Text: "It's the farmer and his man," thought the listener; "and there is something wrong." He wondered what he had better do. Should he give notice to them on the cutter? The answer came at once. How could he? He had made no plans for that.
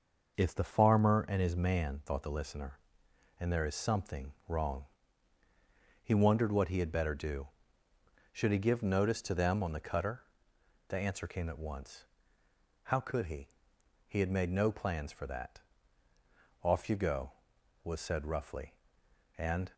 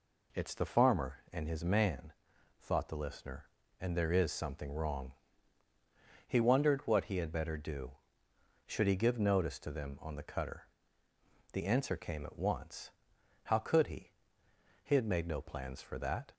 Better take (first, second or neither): second